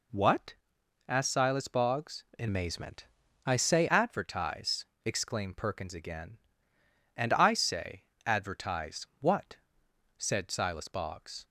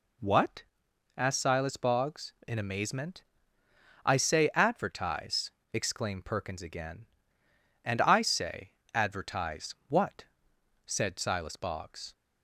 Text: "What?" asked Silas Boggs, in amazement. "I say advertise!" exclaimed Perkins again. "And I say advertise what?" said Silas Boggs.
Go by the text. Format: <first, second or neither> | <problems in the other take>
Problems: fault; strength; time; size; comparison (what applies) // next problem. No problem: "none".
second | changes voice from "amazement" to "say"; from 2.4 to 3.8 s; 1.4 s long // pauses between "say" and "advertise"; slight; at 8.0 s; 0.24 s long; slight in the second